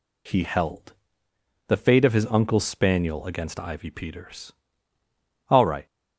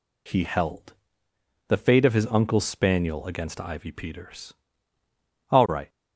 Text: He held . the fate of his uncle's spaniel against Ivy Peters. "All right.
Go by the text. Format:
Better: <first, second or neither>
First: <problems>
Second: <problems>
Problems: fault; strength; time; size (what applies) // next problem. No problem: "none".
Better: neither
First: none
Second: none